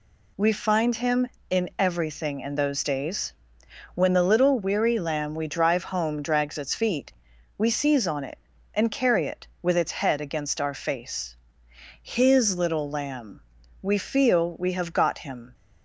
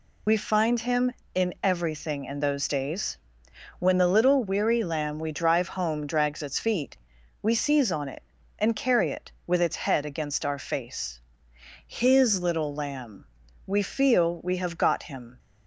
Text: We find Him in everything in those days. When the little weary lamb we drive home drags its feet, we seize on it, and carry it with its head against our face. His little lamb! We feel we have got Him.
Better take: first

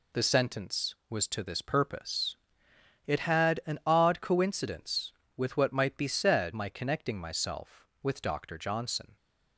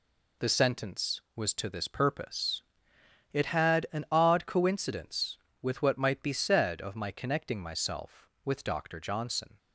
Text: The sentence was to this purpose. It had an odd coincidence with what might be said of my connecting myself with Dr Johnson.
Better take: second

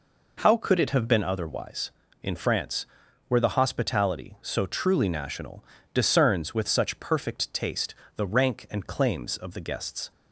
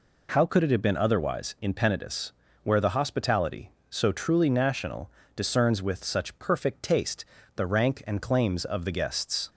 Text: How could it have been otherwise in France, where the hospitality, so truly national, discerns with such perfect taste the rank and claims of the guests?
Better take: first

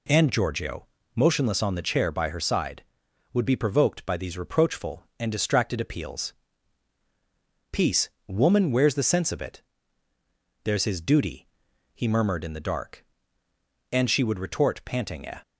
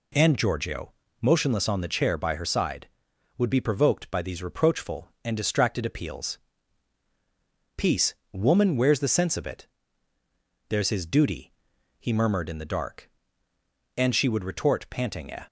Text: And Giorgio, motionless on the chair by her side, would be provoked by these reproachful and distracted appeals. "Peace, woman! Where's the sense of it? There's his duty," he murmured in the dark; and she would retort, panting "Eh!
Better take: neither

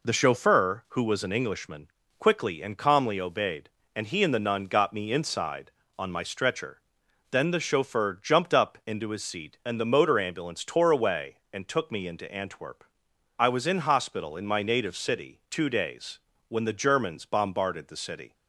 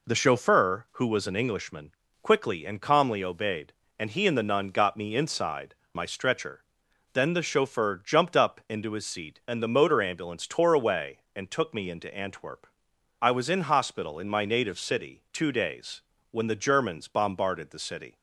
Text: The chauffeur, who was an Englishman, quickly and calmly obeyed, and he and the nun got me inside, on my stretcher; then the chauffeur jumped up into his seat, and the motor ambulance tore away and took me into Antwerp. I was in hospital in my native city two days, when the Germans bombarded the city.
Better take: first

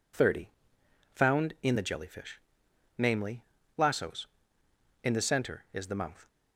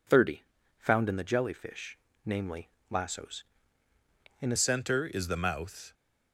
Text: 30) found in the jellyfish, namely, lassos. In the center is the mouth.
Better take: first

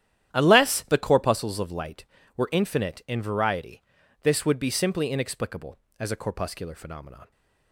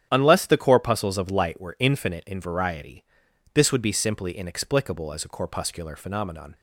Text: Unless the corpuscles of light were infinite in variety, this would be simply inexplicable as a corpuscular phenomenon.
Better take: neither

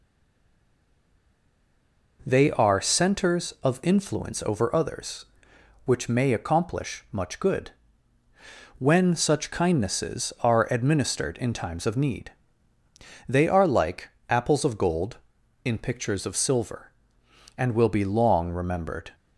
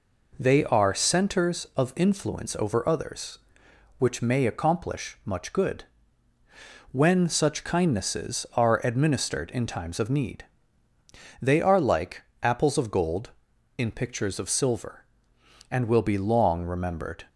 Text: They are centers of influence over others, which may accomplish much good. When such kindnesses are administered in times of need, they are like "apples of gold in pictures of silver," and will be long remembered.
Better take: second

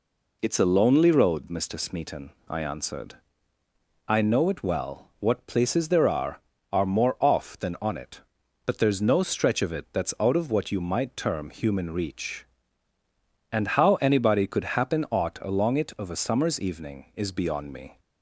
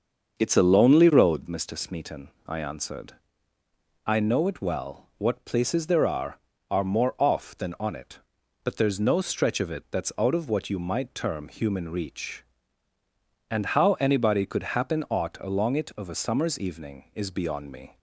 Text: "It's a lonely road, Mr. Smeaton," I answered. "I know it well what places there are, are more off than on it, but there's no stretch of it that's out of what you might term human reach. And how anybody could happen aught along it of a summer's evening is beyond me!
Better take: first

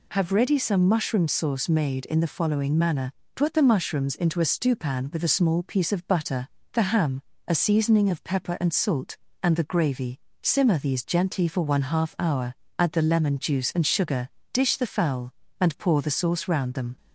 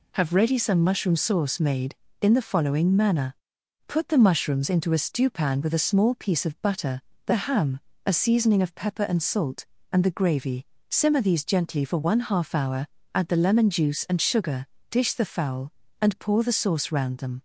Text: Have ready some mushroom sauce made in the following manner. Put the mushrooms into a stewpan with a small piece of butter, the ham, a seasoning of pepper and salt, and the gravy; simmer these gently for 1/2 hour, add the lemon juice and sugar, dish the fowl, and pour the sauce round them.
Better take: neither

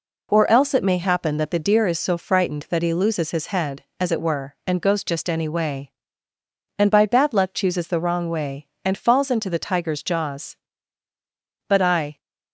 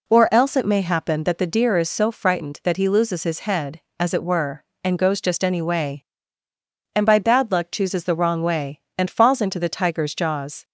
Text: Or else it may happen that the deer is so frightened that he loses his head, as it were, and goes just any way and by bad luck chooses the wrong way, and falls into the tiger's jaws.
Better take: second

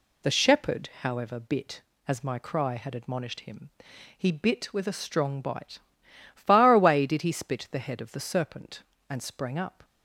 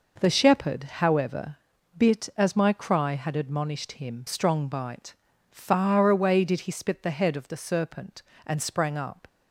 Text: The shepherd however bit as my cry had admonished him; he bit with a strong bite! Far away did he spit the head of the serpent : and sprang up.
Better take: first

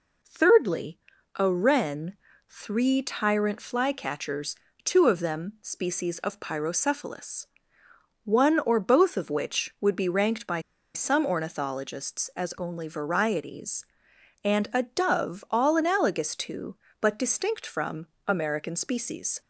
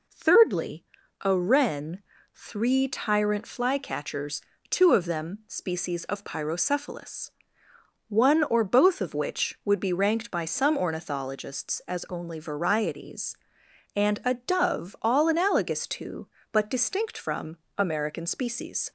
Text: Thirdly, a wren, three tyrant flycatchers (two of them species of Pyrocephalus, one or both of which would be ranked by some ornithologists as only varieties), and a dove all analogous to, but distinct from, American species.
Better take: second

